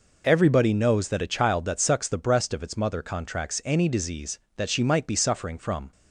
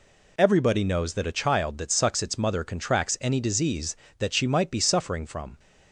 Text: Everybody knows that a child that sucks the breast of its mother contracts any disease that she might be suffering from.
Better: first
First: none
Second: skips "the breast of"; at 2.2 s

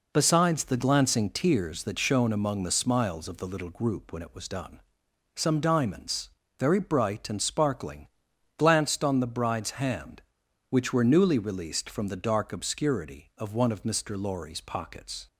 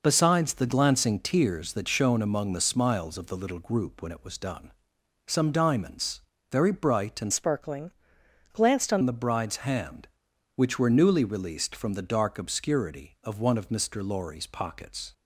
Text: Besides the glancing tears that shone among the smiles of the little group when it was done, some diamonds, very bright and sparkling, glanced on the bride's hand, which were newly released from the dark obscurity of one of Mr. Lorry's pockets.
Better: first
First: none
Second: changes voice from "sparkling" to "on"; from 7.3 to 9.0 s; 1.7 s long

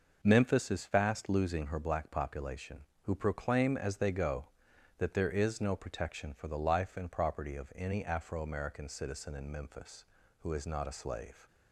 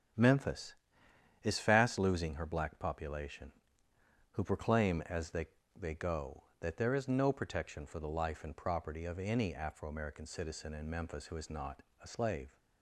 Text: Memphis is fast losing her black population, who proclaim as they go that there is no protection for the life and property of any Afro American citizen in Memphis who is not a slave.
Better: first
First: none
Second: starts louder than the rest; strong; until 1.8 s; 8 dB // says "they" twice; at 5.7 s // pauses between "not" and "a"; slight; at 11.8 s; 0.18 s long

